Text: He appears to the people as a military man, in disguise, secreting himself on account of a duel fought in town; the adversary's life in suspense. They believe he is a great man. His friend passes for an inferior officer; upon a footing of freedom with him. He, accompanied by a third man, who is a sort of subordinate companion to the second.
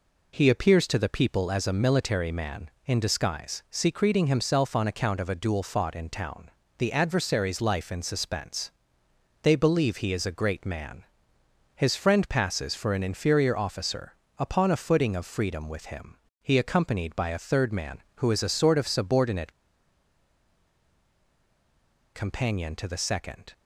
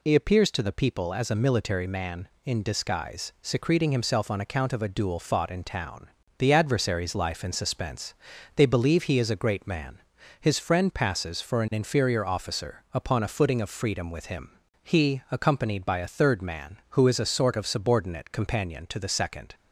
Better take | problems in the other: second | pauses between "subordinate" and "companion"; strong; at 19.5 s; 2.6 s long

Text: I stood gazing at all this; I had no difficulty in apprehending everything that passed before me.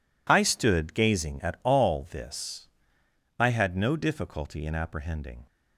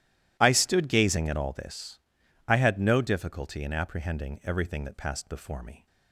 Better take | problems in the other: second | stops before "everything that passed before me"; at 5.4 s

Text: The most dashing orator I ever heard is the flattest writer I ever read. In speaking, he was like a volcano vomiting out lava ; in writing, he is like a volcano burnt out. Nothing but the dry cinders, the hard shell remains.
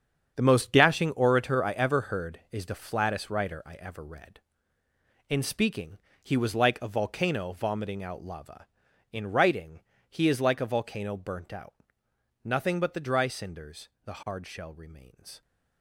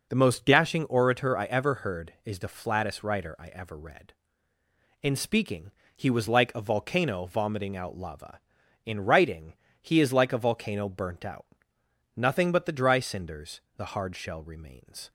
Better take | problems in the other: second | gets quieter; strong; throughout; 12 dB

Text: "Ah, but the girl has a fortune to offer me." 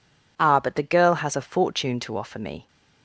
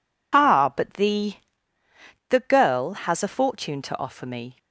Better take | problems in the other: first | says "the" twice; at 2.2 s

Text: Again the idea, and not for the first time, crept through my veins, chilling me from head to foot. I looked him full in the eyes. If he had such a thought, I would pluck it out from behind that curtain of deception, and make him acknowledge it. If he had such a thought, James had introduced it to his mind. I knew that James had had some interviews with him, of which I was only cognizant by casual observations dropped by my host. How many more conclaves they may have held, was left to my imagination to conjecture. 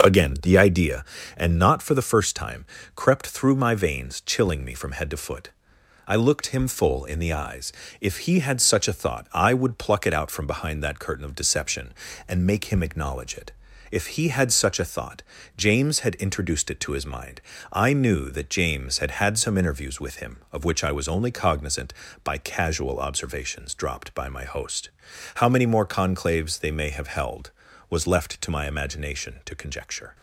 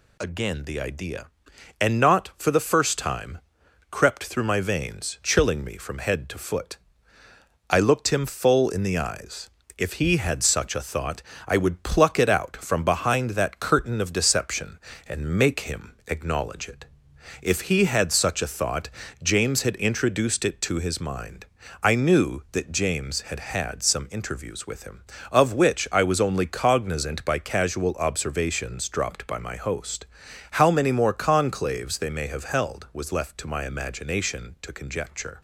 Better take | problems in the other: neither | none

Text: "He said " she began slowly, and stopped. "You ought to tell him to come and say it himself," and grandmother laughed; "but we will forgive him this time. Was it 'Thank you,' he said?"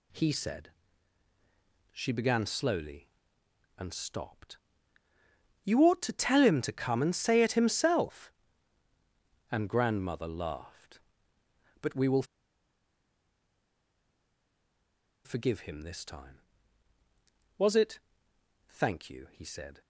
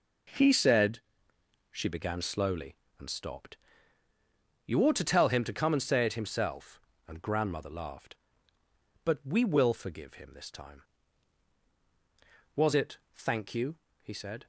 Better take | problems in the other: second | pauses between "will" and "forgive"; strong; at 12.2 s; 3.0 s long // pauses between "it" and "Thank"; noticeable; at 17.9 s; 0.70 s long

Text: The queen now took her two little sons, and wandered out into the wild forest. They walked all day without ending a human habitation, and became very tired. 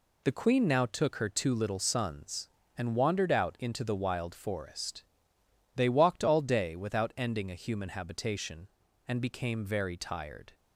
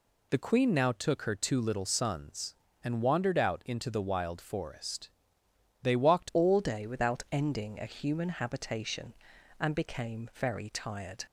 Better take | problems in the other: first | changes voice at "all"; from 6.3 s on; 4.9 s long

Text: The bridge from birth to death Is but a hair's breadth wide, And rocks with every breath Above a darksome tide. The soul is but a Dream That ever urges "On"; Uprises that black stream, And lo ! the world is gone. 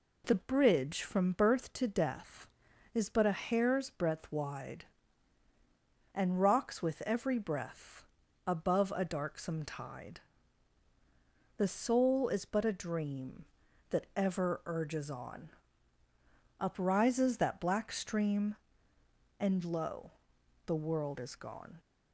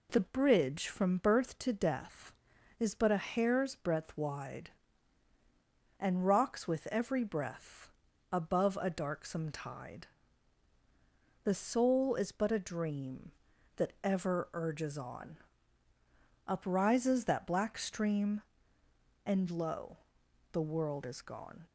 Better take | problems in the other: neither | pauses between "breath" and "Above"; the same in both

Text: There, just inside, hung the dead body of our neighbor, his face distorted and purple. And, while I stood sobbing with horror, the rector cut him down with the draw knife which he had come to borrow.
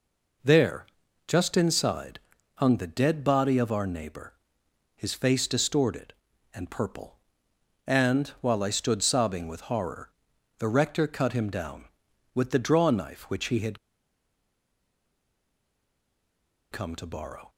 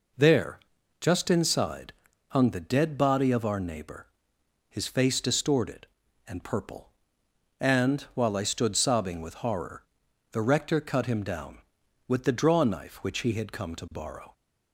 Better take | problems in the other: second | pauses between "had" and "come"; strong; at 13.7 s; 2.9 s long

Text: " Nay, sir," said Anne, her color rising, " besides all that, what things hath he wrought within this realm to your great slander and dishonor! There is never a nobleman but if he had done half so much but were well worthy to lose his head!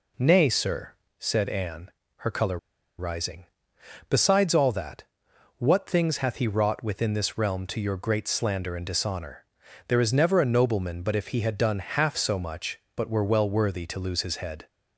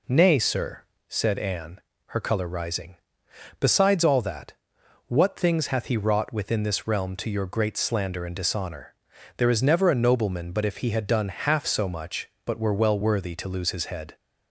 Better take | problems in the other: second | pauses between "color" and "rising"; at 2.5 s; 0.41 s long

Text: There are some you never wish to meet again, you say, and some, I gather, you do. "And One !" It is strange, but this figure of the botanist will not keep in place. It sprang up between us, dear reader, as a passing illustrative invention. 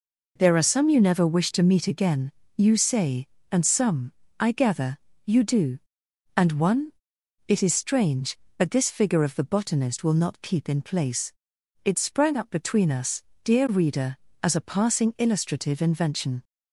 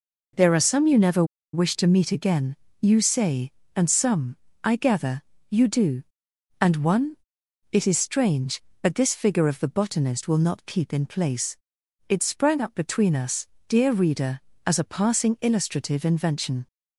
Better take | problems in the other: first | pauses between "never" and "wish"; slight; at 1.2 s; 0.29 s long

